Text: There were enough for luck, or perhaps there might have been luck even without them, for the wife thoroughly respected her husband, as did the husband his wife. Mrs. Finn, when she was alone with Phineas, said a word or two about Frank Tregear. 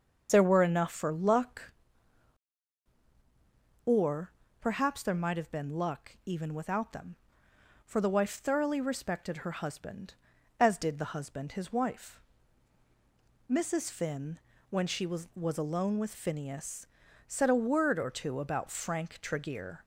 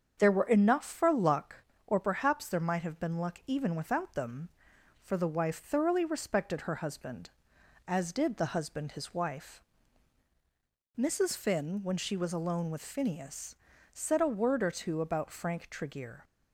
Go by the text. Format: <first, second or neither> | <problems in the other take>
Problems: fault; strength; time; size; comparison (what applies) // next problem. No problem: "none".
second | starts louder than the rest; until 1.3 s; 6.5 dB; strong in the second // pauses between "or" and "perhaps"; slight; at 4.3 s; 0.30 s long // says "was" twice; at 15.3 s